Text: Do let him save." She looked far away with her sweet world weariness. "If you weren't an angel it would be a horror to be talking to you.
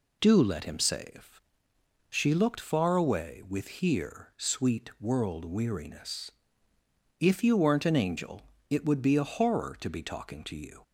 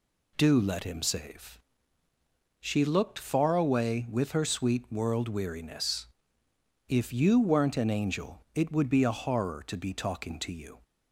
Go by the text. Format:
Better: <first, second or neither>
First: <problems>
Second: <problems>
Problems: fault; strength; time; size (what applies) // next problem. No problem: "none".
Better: second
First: says "here" for "her"; at 3.6 s // pauses between "angel" and "it"; slight; at 8.4 s; 0.26 s long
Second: none